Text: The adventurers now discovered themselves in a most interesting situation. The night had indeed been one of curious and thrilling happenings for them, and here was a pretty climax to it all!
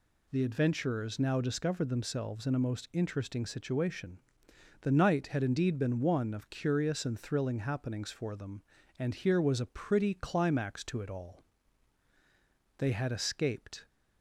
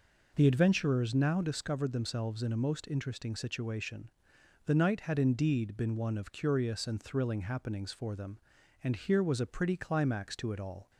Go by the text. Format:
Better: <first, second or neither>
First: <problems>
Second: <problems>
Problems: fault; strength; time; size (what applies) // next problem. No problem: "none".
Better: second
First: goes on to say "They had escaped"; noticeable; from 12.7 s on; 1.1 s long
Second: none